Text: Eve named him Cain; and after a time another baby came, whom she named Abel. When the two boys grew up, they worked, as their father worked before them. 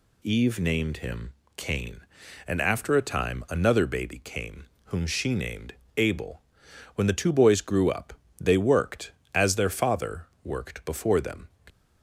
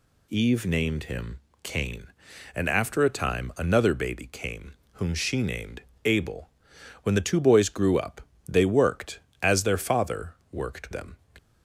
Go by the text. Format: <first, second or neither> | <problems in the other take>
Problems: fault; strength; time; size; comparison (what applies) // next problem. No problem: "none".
first | pauses between "him" and "Cain"; slight; at 1.3 s; 0.24 s long; slight in the first // pauses between "named" and "Abel"; slight; at 5.8 s; 0.24 s long; slight in the first // pauses between "father" and "worked"; slight; at 10.3 s; 0.18 s long; slight in the first // skips "before"; at 10.9 s